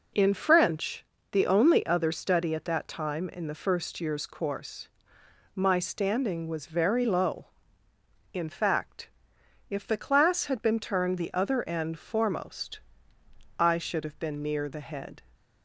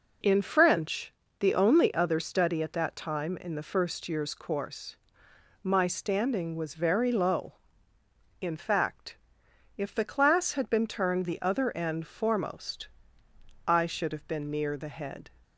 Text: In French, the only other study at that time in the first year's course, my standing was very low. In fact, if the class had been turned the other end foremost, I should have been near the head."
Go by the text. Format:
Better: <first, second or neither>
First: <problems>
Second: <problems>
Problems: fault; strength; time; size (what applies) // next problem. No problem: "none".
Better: neither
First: none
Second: none